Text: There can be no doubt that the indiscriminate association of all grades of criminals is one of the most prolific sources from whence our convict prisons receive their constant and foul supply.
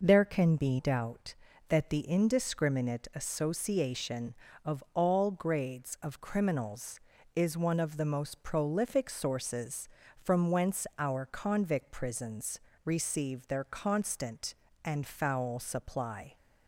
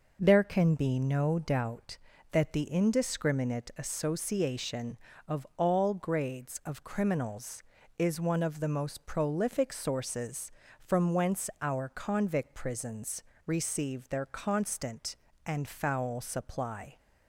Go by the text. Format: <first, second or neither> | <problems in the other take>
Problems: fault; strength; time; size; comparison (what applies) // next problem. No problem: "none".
second | skips "no"; at 0.7 s // pauses between "prisons" and "receive"; slight; at 12.5 s; 0.26 s long; slight in the second